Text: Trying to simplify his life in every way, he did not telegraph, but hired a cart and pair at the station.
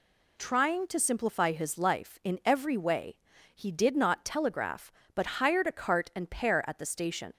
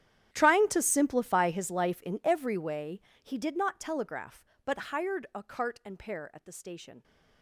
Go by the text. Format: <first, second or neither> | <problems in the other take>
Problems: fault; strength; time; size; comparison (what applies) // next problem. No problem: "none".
first | gets quieter; strong; throughout; 21 dB